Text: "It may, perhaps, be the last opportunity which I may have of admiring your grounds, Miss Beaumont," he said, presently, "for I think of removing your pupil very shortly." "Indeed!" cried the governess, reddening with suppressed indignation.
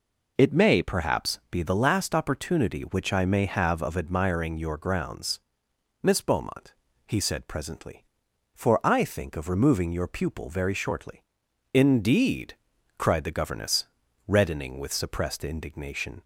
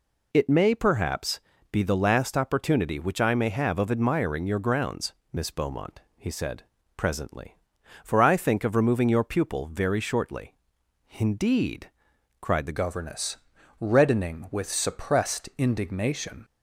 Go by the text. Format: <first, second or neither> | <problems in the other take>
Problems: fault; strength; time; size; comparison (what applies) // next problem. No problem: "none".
first | changes voice at "governess"; from 12.7 s on; 3.7 s long